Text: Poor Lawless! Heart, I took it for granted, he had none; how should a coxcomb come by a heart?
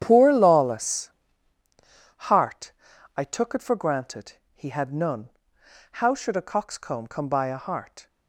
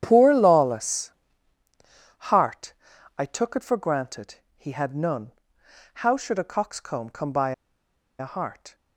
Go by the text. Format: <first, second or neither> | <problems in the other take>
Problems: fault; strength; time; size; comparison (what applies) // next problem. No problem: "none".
first | starts louder than the rest; strong; until 1.0 s; 9.5 dB; strong in the first // pauses between "by" and "a"; noticeable; at 7.5 s; 0.67 s long